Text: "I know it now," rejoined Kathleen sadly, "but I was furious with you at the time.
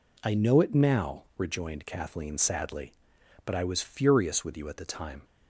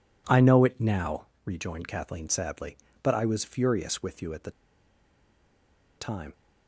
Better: first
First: none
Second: pauses between "the" and "time"; strong; at 4.4 s; 1.4 s long

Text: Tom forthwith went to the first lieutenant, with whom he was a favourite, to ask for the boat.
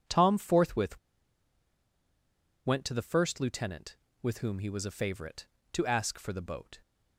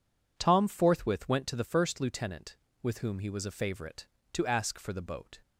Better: second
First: pauses between "forthwith" and "went"; strong; at 0.9 s; 1.6 s long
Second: none

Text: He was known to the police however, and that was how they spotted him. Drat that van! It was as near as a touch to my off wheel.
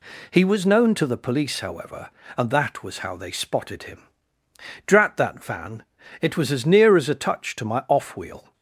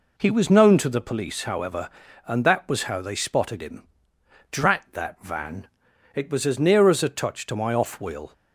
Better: neither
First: none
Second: none

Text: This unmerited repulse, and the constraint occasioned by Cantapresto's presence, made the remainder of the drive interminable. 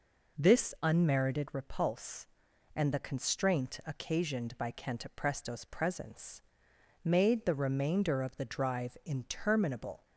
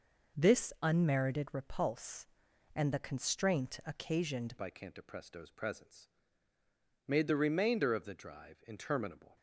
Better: first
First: none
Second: changes voice at "by"; from 4.5 s on; 4.8 s long

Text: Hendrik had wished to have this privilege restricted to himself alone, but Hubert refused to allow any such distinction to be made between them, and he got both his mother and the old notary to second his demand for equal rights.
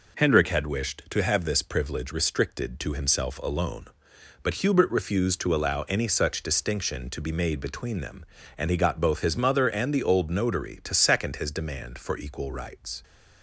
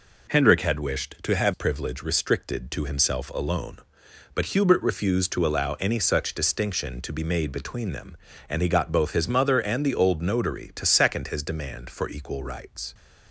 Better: first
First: none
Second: skips "this"; at 1.5 s

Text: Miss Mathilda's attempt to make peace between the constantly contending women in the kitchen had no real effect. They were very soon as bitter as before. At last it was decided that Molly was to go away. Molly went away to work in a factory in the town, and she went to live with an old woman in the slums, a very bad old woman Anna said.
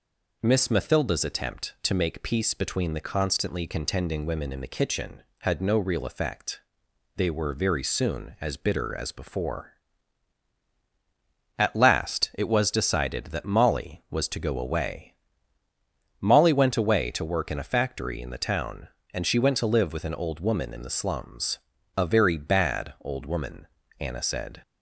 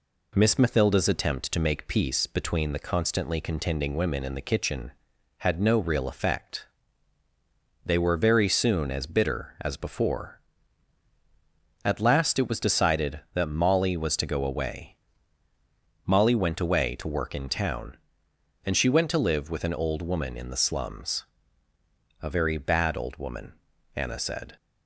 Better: first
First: pauses between "woman" and "Anna"; slight; at 23.6 s; 0.32 s long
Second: skips "a factory in the"; at 17.4 s // pauses between "woman" and "Anna"; at 23.5 s; 0.42 s long

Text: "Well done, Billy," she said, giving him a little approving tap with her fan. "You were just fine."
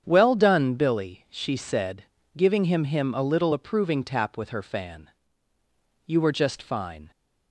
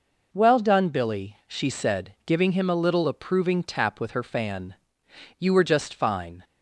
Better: second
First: starts louder than the rest; strong; until 1.0 s; 8 dB // says "him" twice; at 2.8 s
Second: none

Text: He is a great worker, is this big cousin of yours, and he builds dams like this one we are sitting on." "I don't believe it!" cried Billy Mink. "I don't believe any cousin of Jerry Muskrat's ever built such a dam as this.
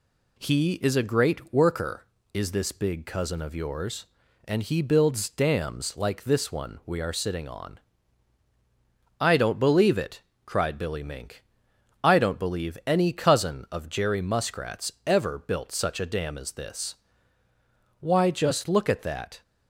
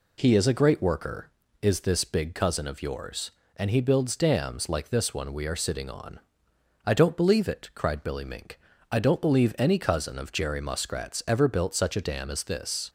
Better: second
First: goes on to say "Why just look at that"; from 17.9 s on; 1.4 s long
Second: none

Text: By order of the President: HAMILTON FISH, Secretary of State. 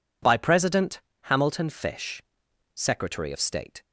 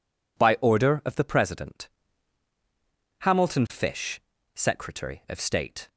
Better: second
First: skips "order of the"; at 0.3 s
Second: none

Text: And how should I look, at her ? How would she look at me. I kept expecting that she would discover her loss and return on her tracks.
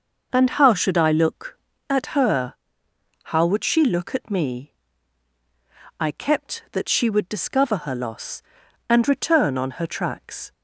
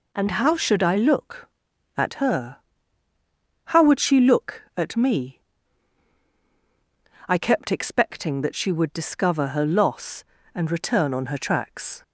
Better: second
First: skips "expecting"; at 6.6 s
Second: none

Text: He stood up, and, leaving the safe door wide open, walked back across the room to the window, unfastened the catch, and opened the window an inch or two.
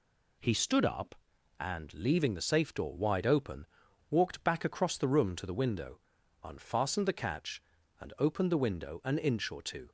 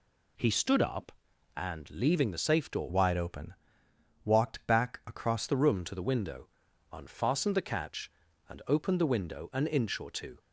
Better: first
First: none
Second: changes voice from "wide" to "across"; from 2.8 to 5.4 s; 2.6 s long

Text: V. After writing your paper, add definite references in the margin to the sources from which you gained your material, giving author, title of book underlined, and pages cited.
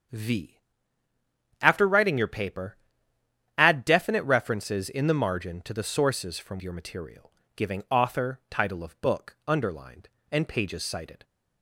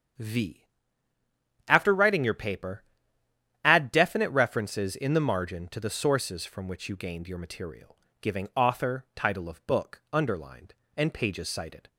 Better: second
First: starts louder than the rest; strong; until 2.1 s; 7 dB // skips "which you gained"; at 6.6 s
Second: starts louder than the rest; strong; until 2.2 s; 7.5 dB

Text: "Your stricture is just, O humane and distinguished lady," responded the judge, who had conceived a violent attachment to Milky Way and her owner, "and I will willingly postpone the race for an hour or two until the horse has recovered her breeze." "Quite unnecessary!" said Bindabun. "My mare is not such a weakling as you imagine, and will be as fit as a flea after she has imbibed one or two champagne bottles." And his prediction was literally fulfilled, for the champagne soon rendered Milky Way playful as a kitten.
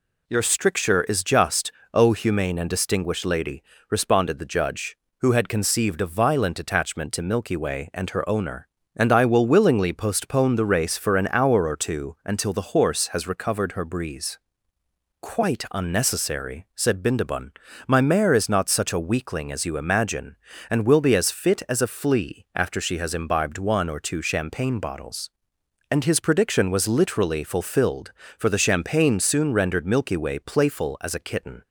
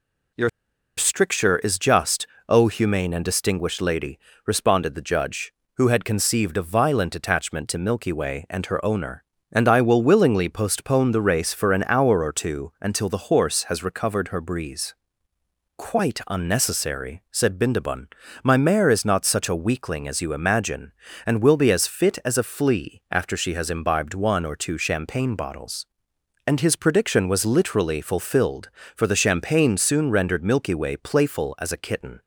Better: first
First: none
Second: pauses between "Your" and "stricture"; noticeable; at 0.4 s; 0.48 s long

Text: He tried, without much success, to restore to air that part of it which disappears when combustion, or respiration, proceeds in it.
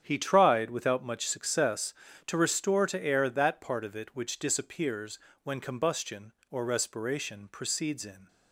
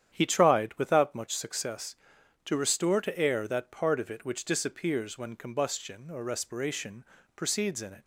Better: second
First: starts louder than the rest; strong; until 1.0 s; 8.5 dB // pauses between "disappears" and "when"; slight; at 5.1 s; 0.26 s long // stops before "it"; at 8.2 s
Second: starts louder than the rest; strong; until 1.1 s; 9.5 dB

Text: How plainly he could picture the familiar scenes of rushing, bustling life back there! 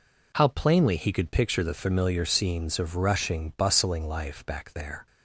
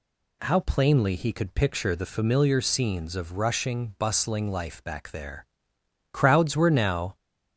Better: first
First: none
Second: goes on to say "Crowds were now"; noticeable; from 6.1 s on; 1.0 s long

